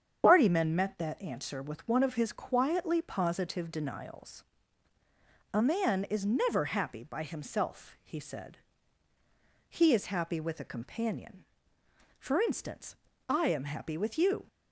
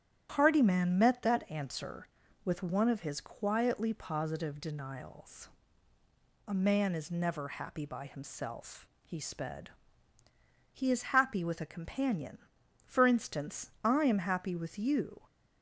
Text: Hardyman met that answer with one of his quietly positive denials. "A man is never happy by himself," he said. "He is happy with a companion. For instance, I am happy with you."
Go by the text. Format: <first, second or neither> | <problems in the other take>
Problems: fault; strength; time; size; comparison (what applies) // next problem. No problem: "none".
first | starts louder than the rest; strong; until 1.3 s; 10.5 dB; strong in the first // says "sped" for "said"; at 9.1 s